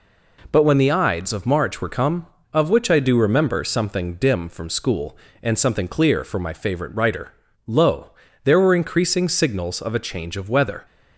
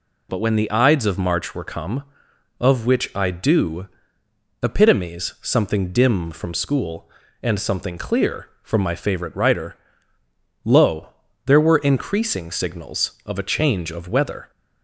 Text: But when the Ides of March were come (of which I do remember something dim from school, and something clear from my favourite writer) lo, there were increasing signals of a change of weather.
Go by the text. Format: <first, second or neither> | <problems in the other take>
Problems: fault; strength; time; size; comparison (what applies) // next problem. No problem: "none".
first | says "epitomes" for "remember"; at 4.6 s